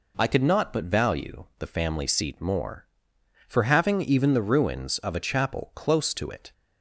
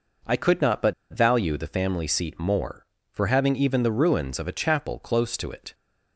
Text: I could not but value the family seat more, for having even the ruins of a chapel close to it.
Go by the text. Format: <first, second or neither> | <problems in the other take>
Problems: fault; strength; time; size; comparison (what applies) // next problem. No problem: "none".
first | pauses between "but" and "value"; slight; at 0.9 s; 0.18 s long